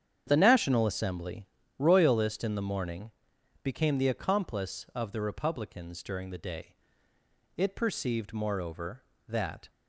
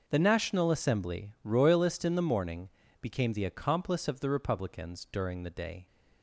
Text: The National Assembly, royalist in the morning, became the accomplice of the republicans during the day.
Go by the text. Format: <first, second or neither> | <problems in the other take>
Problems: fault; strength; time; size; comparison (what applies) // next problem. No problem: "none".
second | starts louder than the rest; strong; until 1.2 s; 8.5 dB; noticeable in the second // goes on to say "It perceived moreover that"; strong; from 7.5 s on; 2.1 s long